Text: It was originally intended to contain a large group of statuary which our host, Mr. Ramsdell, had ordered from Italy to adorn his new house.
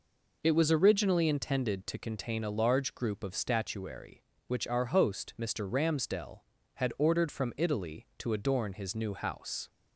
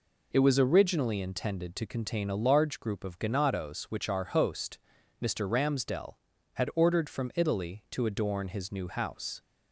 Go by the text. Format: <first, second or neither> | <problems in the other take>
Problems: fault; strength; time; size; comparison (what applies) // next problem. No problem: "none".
first | says "ganados" for "statuary"; at 3.1 s